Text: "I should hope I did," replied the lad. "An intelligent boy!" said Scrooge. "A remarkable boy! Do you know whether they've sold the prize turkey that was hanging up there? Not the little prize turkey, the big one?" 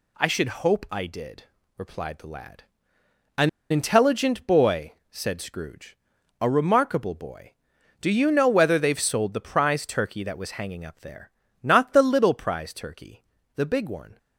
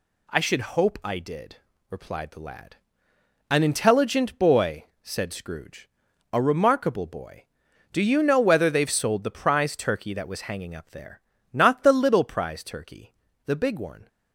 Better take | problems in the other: second | pauses between "An" and "intelligent"; slight; at 3.4 s; 0.21 s long

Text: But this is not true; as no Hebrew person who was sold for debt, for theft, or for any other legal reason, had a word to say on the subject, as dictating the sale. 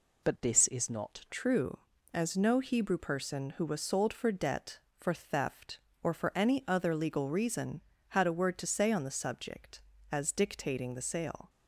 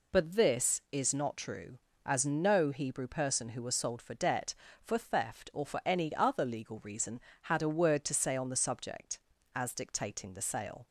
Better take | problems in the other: second | changes voice at "true"; from 1.3 s on; 10.1 s long

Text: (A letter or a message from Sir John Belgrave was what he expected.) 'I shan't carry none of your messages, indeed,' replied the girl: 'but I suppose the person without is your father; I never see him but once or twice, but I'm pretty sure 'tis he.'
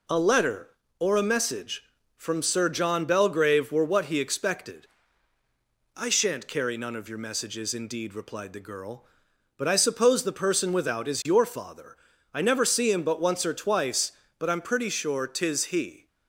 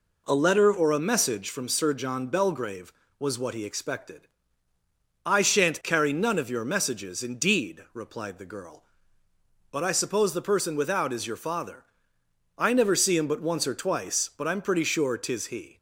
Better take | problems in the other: second | says "were" for "was"; at 3.7 s

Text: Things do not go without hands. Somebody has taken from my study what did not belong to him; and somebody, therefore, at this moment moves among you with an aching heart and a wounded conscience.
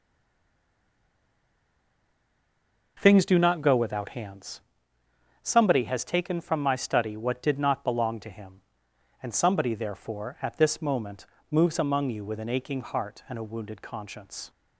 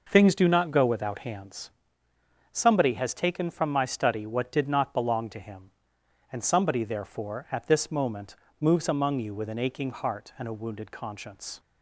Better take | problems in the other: second | stays silent before the first word; strong; until 2.9 s; 2.9 s long // pauses between "moment" and "moves"; slight; at 11.2 s; 0.28 s long; slight in the second

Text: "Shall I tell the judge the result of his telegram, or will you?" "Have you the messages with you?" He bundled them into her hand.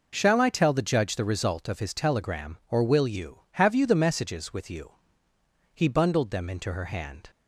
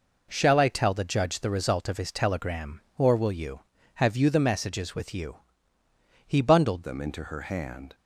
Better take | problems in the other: first | changes voice at "them"; from 6.8 s on; 1.1 s long

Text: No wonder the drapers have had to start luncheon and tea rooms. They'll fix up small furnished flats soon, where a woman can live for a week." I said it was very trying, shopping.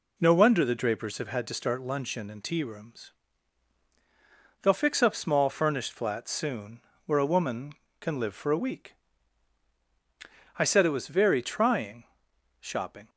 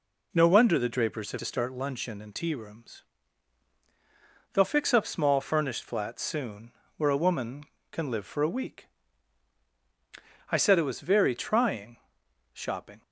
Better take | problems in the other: first | skips "had"; at 1.3 s

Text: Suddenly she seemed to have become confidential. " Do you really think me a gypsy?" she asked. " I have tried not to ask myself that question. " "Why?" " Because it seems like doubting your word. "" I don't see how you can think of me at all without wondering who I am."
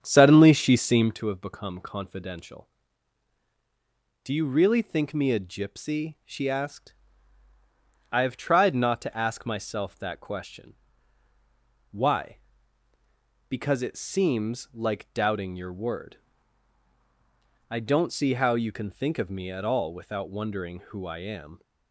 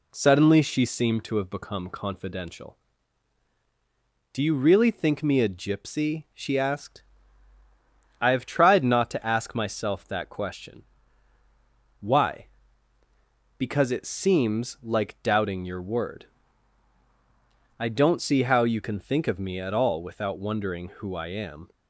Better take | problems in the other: second | starts louder than the rest; strong; until 1.2 s; 8 dB

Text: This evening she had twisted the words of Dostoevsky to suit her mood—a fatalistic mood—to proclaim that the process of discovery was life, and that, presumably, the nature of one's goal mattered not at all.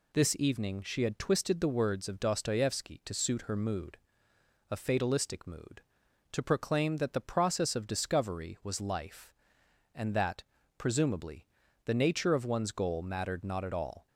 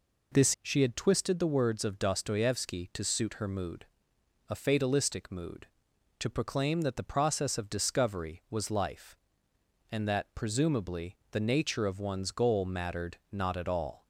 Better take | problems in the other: first | skips "evening"; at 0.5 s

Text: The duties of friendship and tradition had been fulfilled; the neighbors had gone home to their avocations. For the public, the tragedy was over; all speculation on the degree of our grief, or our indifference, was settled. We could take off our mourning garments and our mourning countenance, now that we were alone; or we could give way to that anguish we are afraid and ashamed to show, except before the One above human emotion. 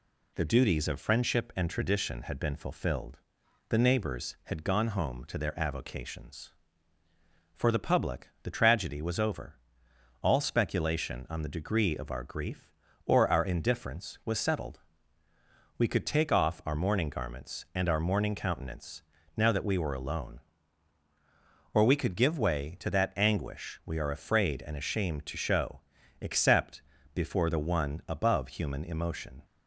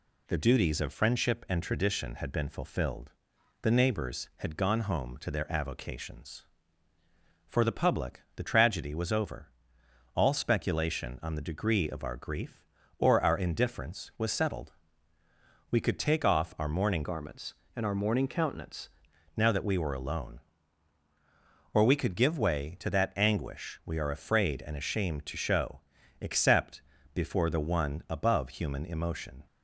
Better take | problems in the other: first | changes voice from "garments" to "countenance"; from 17.0 to 18.8 s; 1.8 s long // pauses between "except" and "before"; slight; at 26.8 s; 0.32 s long; slight in the first

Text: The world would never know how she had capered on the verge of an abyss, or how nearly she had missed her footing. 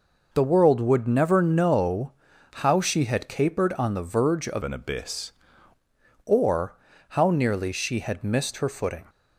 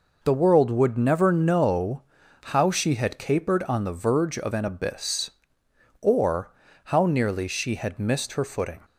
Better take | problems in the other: second | pauses between "know" and "how"; at 2.1 s; 0.42 s long; also in the second // changes voice from "an" to "abyss"; from 4.6 to 5.3 s; 0.7 s long // pauses between "or" and "how"; slight; at 6.7 s; 0.36 s long; slight in the second

